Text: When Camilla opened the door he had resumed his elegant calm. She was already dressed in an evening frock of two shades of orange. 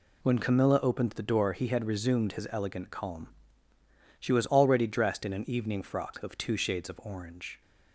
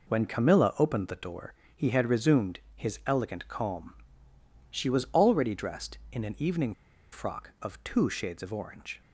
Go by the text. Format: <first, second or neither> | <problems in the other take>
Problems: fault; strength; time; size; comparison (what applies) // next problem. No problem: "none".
first | pauses between "door" and "he"; slight; at 1.5 s; 0.22 s long // pauses between "resumed" and "his"; slight; at 2.6 s; 0.16 s long // pauses between "evening" and "frock"; at 6.7 s; 0.39 s long